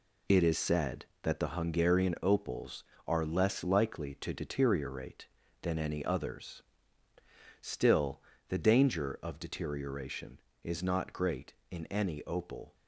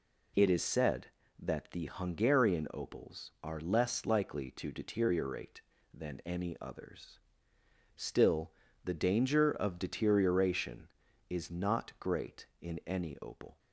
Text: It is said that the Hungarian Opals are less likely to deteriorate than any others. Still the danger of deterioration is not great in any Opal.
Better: second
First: gets quieter; strong; throughout; 8 dB // pauses between "Still" and "the"; slight; at 8.2 s; 0.28 s long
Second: pauses between "Still" and "the"; slight; at 8.5 s; 0.32 s long

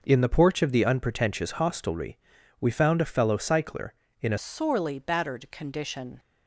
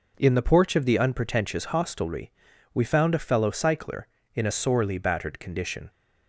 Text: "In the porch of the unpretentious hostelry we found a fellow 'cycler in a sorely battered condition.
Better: second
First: pauses between "hostelry" and "we"; at 2.1 s; 0.42 s long // changes voice at "sorely"; from 4.3 s on; 1.8 s long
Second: pauses between "hostelry" and "we"; at 2.3 s; 0.42 s long

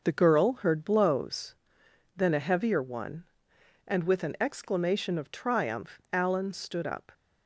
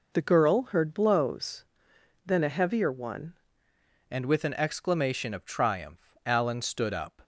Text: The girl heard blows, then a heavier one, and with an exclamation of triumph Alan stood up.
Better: first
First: none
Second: changes voice at "and"; from 4.1 s on; 3.1 s long

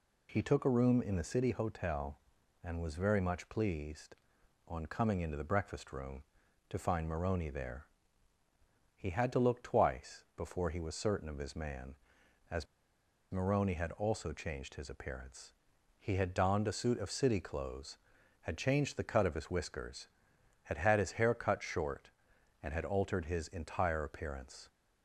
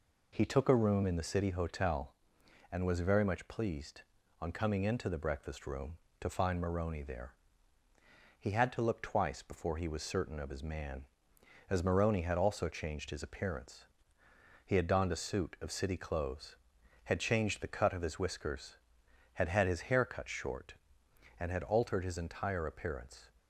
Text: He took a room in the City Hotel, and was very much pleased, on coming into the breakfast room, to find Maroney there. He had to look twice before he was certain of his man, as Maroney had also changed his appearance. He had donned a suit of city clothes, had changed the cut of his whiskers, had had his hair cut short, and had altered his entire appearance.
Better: second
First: pauses between "as" and "Maroney"; noticeable; at 12.6 s; 0.67 s long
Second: none

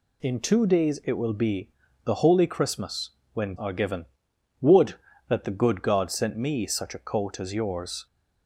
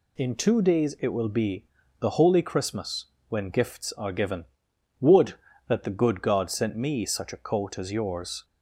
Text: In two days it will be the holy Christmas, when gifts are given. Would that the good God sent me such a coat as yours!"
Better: second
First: pauses between "be" and "the"; slight; at 1.7 s; 0.34 s long // skips "gifts"; at 3.5 s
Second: pauses between "be" and "the"; slight; at 1.6 s; 0.34 s long

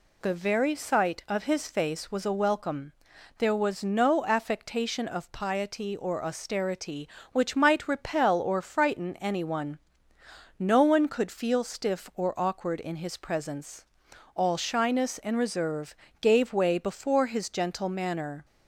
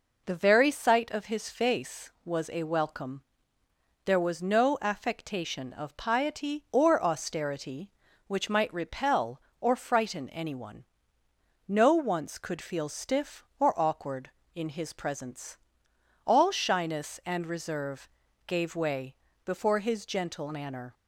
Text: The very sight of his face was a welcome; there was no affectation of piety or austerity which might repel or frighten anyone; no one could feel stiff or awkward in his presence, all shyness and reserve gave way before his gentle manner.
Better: first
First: pauses between "reserve" and "gave"; slight; at 15.9 s; 0.26 s long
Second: says "once" for "one"; at 11.9 s // pauses between "reserve" and "gave"; at 18.0 s; 0.38 s long // pauses between "way" and "before"; slight; at 19.1 s; 0.28 s long

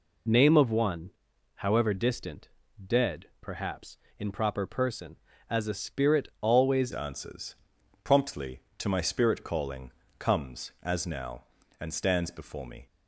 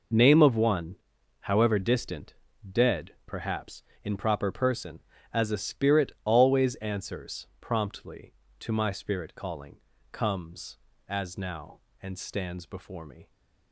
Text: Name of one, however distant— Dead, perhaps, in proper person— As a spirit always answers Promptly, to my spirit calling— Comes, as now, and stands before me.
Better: second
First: changes voice at "answers"; from 6.9 s on; 5.9 s long // pauses between "answers" and "Promptly"; noticeable; at 7.5 s; 0.48 s long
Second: none

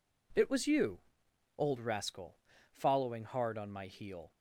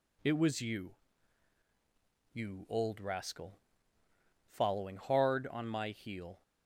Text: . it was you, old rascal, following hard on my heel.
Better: first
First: none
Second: says "you" twice; at 2.3 s

